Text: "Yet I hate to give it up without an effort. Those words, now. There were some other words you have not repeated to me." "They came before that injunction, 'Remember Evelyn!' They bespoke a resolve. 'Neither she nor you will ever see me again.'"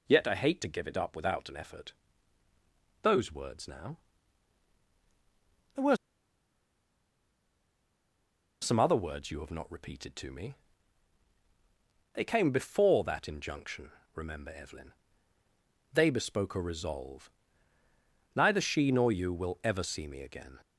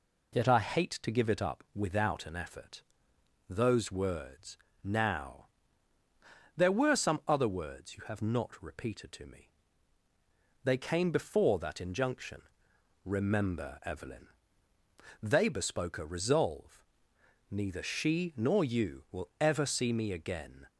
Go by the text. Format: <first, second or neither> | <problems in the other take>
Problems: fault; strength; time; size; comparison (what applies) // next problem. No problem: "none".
second | pauses between "were" and "some"; strong; at 5.9 s; 2.6 s long